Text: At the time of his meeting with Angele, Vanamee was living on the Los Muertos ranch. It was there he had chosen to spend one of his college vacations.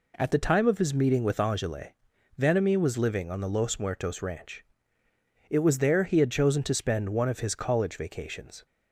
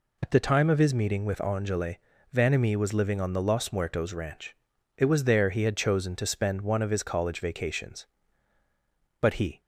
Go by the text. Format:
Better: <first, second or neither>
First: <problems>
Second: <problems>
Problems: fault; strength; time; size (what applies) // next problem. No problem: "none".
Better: first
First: none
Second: goes on to say "But he"; slight; from 9.2 s on; 0.40 s long